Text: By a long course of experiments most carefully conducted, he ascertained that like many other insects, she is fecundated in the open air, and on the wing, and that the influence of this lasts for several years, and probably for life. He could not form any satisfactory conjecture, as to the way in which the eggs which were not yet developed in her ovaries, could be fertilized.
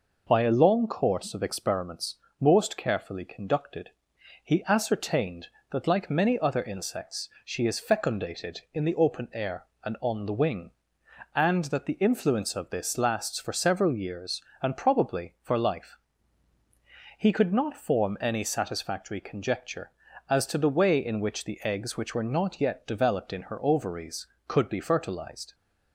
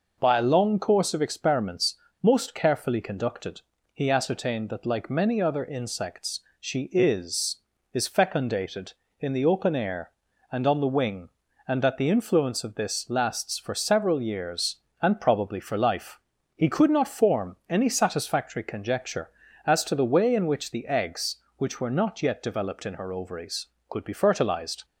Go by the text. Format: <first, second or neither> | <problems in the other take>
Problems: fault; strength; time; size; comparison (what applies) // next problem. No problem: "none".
first | pauses between "experiments" and "most"; slight; at 1.9 s; 0.26 s long; slight in the first // says "is" twice; at 7.9 s